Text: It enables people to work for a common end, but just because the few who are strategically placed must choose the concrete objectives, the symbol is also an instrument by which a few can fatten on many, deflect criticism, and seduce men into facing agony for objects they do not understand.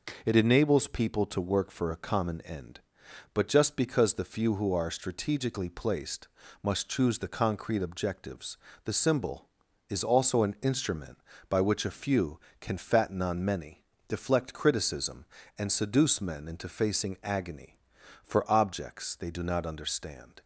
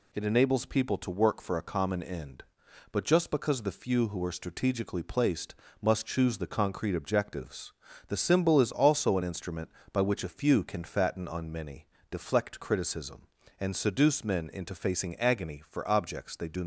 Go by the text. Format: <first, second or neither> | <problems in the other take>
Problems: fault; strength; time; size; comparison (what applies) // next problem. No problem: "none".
first | pauses between "placed" and "must"; slight; at 5.5 s; 0.26 s long; slight in the first // stops before "not understand"; at 16.6 s